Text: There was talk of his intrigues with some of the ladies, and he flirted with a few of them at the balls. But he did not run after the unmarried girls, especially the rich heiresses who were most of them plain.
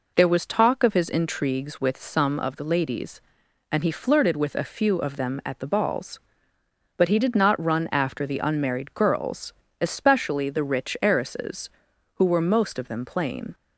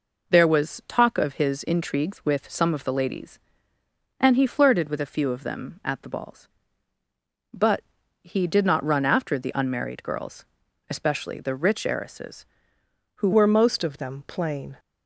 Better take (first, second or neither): first